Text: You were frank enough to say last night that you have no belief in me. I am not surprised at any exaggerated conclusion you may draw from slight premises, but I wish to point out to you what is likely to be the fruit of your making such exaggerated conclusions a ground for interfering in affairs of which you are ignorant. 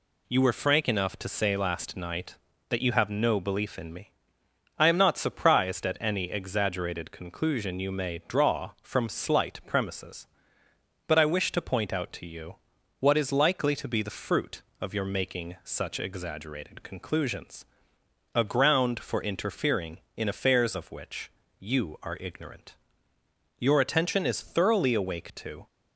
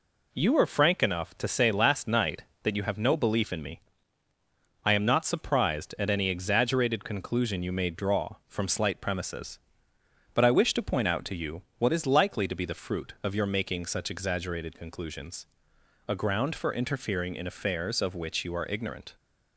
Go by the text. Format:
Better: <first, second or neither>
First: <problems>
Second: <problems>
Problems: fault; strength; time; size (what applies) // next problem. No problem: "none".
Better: second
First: pauses between "you" and "what"; at 12.5 s; 0.44 s long // pauses between "conclusions" and "a"; noticeable; at 17.6 s; 0.70 s long // pauses between "which" and "you"; slight; at 21.3 s; 0.28 s long // goes on to say "Your attention is thoroughly awake to"; strong; from 23.5 s on; 2.0 s long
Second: pauses between "you" and "what"; slight; at 11.6 s; 0.16 s long // pauses between "conclusions" and "a"; noticeable; at 15.4 s; 0.62 s long